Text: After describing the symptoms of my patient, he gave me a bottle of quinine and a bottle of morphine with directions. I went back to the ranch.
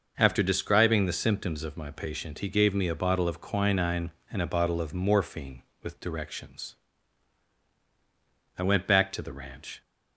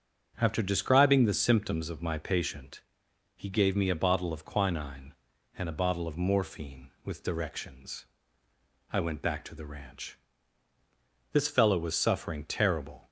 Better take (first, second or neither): first